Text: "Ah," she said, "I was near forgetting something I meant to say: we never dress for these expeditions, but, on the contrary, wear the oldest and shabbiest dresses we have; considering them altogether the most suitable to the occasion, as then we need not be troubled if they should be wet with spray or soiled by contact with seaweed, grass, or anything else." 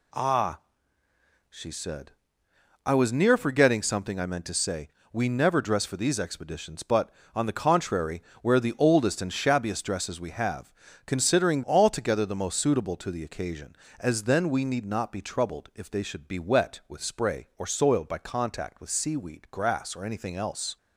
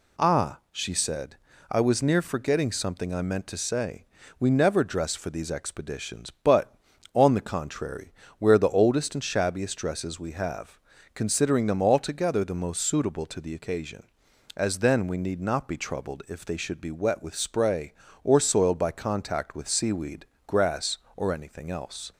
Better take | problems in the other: second | skips "them"; at 11.6 s

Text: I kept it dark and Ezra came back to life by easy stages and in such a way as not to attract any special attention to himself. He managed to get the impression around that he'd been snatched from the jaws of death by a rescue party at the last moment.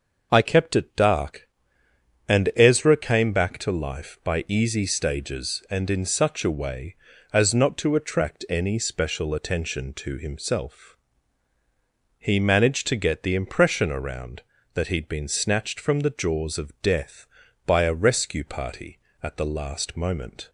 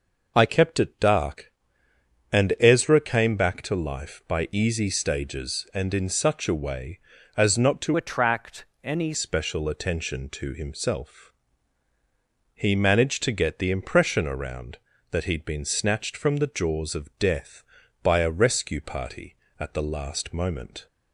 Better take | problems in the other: first | changes voice from "attract" to "any"; from 7.9 to 9.1 s; 1.2 s long // pauses between "attract" and "any"; slight; at 8.6 s; 0.18 s long

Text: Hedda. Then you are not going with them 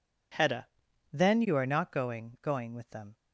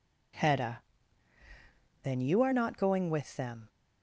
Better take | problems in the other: second | says "going" twice; at 2.4 s

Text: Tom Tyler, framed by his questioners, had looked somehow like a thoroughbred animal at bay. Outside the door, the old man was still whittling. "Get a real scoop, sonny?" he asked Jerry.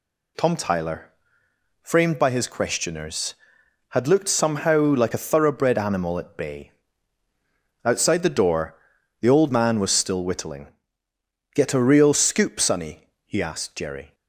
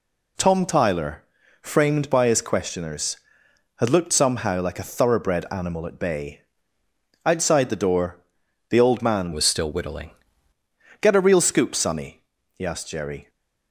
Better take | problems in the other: first | changes voice from "was" to "whittling"; from 9.3 to 10.1 s; 0.8 s long

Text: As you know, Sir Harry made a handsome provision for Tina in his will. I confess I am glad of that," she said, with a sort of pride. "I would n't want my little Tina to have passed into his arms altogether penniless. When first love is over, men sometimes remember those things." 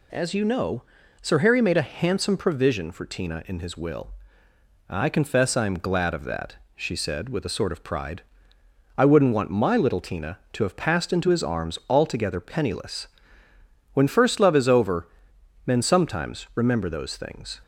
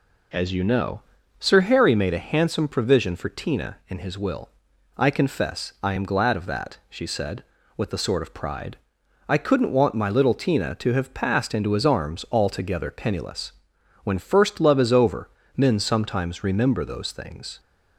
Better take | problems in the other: first | says "could" for "would"; at 9.3 s

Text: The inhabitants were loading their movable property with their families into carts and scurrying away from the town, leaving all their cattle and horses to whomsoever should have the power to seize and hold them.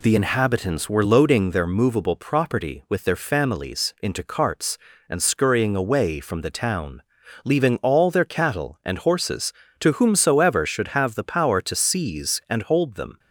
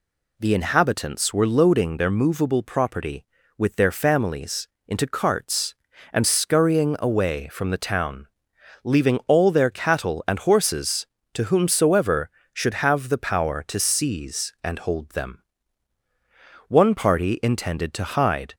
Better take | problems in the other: first | pauses between "families" and "into"; slight; at 4.6 s; 0.18 s long // goes on to say "One party intended to hide"; strong; from 16.6 s on; 1.8 s long

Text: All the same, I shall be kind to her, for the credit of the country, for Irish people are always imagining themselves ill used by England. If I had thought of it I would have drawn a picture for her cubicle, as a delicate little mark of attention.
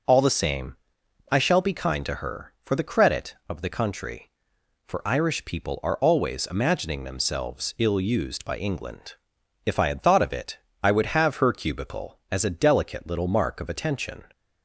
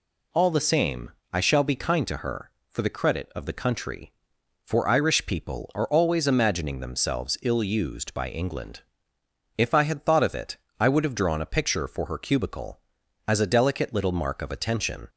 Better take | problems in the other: second | pauses between "it" and "I"; slight; at 10.5 s; 0.26 s long; slight in the second // skips "drawn a picture for"; at 11.3 s

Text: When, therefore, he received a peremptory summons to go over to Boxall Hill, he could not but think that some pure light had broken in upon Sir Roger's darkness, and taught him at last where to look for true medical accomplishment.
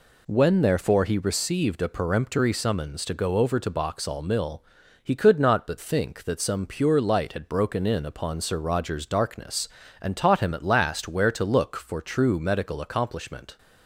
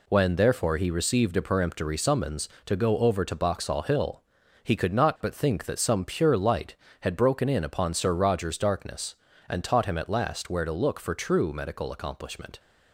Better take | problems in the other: second | says "Mill" for "Hill"; at 4.2 s

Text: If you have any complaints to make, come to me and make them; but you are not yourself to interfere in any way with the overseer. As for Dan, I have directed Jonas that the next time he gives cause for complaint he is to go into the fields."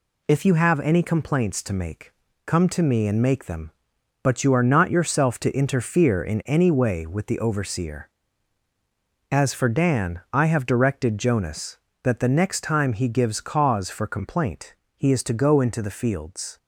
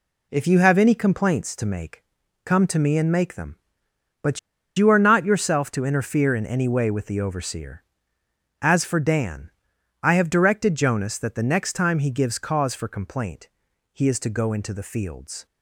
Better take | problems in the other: first | pauses between "but" and "you"; at 4.3 s; 0.39 s long // pauses between "complaint" and "he"; noticeable; at 13.4 s; 0.46 s long; slight in the first

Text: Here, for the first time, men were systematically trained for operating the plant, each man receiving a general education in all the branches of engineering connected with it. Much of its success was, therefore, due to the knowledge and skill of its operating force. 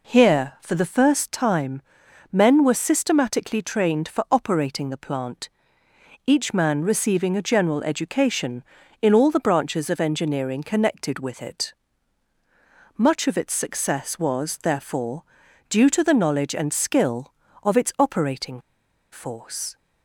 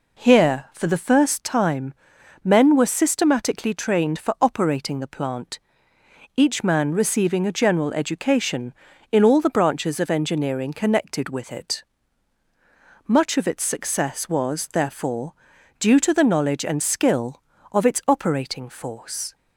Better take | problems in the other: second | pauses between "operating" and "force"; noticeable; at 18.5 s; 0.52 s long

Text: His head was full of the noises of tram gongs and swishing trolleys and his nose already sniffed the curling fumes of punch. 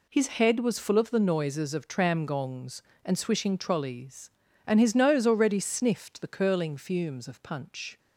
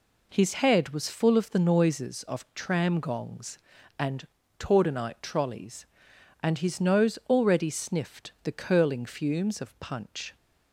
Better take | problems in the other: first | says "tordenite" for "swishing"; at 4.5 s

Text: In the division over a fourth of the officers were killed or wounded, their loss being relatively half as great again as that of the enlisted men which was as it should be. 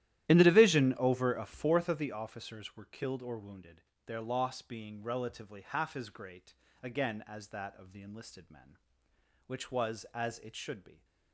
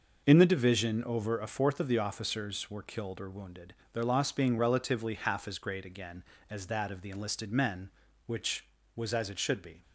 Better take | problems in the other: second | starts louder than the rest; strong; until 2.2 s; 13 dB // pauses between "great" and "again"; slight; at 6.5 s; 0.26 s long

